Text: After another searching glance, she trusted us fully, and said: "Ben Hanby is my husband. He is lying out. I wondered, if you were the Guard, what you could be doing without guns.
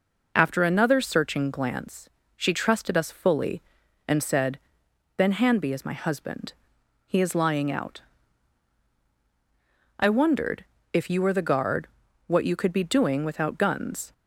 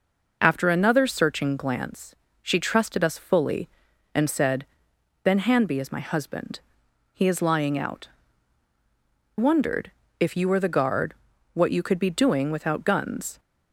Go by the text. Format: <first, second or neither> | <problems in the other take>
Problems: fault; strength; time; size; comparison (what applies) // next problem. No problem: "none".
first | skips "I"; at 8.7 s